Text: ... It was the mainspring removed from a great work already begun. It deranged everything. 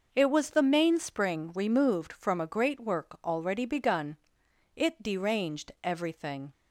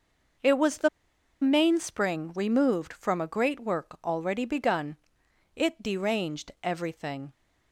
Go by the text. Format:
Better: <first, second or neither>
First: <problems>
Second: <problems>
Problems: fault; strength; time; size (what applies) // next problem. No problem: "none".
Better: first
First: none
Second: pauses between "the" and "mainspring"; noticeable; at 0.8 s; 0.52 s long